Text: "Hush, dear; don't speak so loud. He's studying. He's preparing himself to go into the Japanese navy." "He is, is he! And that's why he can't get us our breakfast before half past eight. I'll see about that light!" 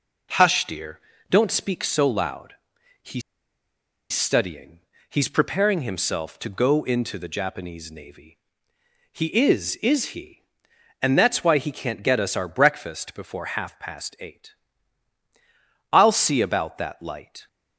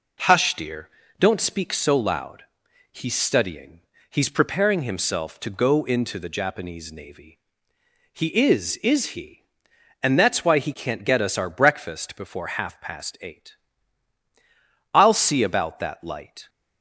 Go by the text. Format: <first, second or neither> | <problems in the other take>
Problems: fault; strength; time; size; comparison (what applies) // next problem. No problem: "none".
second | pauses between "He's" and "studying"; noticeable; at 3.2 s; 0.91 s long